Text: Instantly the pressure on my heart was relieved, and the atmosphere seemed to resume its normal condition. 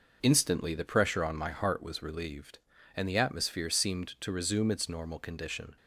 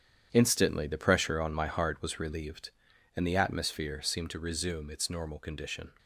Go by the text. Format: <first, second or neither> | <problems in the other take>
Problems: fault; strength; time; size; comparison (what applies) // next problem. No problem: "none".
first | gets quieter; strong; throughout; 10.5 dB